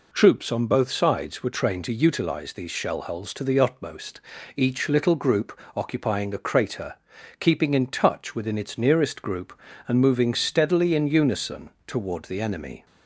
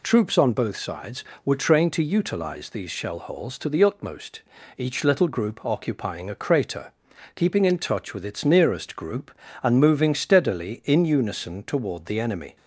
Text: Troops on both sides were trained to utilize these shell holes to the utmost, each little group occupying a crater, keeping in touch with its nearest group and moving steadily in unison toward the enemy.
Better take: second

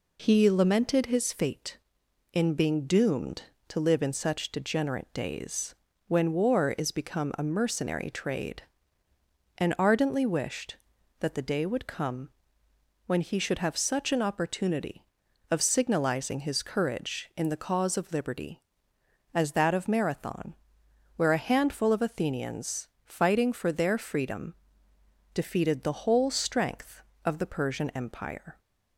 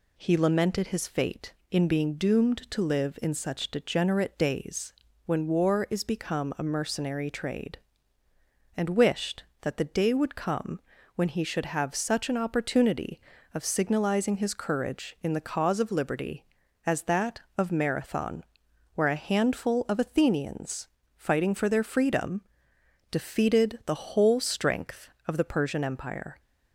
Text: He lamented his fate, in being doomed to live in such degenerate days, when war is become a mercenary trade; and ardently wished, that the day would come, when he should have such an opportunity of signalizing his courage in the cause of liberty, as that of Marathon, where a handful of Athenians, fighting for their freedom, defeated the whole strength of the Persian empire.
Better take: first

